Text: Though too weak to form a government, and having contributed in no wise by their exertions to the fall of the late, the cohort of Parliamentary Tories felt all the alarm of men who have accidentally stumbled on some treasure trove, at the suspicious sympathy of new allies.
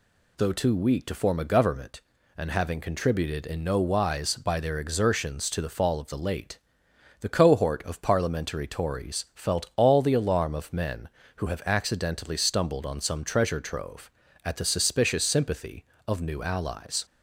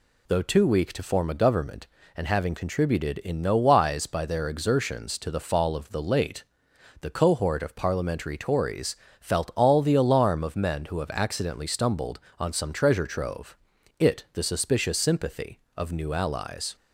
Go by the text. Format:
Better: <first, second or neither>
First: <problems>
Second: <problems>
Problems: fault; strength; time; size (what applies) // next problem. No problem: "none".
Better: first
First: none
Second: pauses between "Tories" and "felt"; slight; at 8.9 s; 0.24 s long // says "it" for "at"; at 13.9 s